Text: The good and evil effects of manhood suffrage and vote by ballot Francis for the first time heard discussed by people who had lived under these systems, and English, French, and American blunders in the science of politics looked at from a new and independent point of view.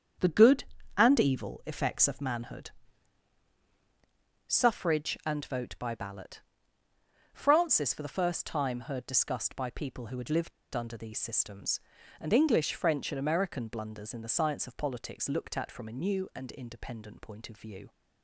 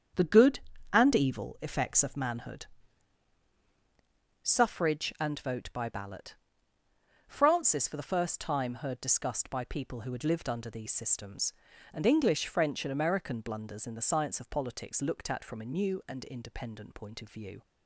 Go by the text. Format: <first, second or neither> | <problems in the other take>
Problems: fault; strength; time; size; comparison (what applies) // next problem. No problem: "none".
second | starts louder than the rest; strong; until 1.5 s; 8 dB; strong in the second // pauses between "manhood" and "suffrage"; strong; at 2.6 s; 1.7 s long; strong in the second // pauses between "ballot" and "Francis"; noticeable; at 6.3 s; 0.94 s long; noticeable in the second // pauses between "lived" and "under"; slight; at 10.5 s; 0.24 s long